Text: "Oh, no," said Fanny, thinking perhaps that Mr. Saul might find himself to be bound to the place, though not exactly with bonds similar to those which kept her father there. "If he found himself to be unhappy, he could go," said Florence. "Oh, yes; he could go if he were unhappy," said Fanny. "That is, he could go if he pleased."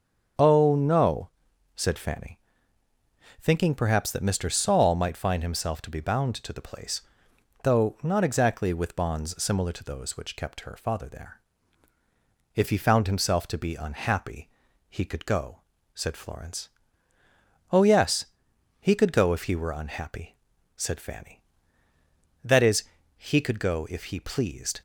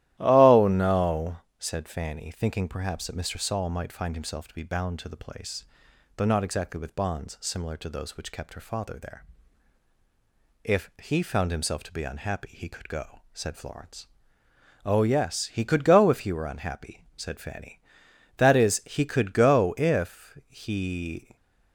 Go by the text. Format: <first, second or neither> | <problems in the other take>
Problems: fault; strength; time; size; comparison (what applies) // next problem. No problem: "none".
first | starts louder than the rest; strong; until 1.2 s; 14 dB; strong in the first // stops before "pleased"; at 21.3 s